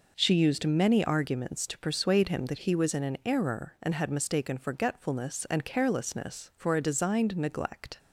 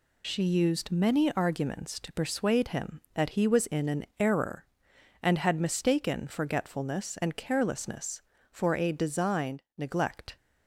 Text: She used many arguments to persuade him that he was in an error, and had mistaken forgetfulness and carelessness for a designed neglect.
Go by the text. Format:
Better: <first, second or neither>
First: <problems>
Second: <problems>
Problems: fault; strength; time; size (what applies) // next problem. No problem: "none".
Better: first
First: none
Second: loses the start of "She"; at 0.2 s; 35 ms